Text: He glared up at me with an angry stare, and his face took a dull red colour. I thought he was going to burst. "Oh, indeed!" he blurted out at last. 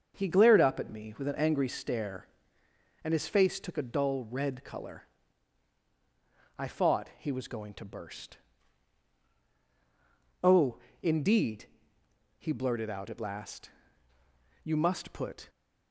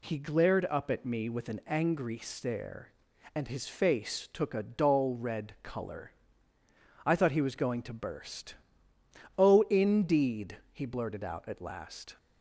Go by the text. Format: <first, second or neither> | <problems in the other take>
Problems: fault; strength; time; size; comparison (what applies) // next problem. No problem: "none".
second | starts louder than the rest; until 1.2 s; 6.5 dB // goes on to say "You must put"; noticeable; from 14.6 s on; 0.86 s long